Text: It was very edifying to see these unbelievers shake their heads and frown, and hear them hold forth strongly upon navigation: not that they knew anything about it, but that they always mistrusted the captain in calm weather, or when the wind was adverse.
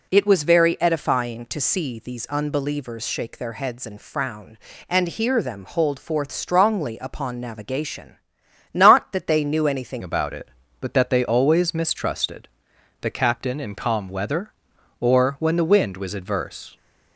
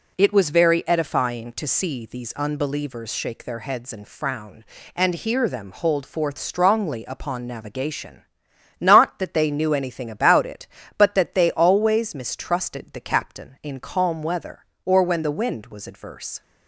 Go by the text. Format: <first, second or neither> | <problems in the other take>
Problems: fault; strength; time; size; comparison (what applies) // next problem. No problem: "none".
second | changes voice at "about"; from 10.0 s on; 6.7 s long // pauses between "mistrusted" and "the"; noticeable; at 12.4 s; 0.54 s long